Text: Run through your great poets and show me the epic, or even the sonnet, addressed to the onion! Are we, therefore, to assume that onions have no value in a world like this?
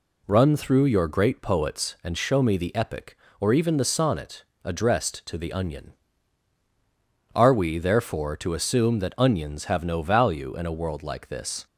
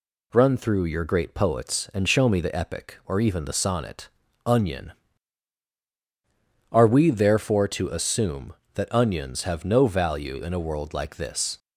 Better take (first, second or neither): first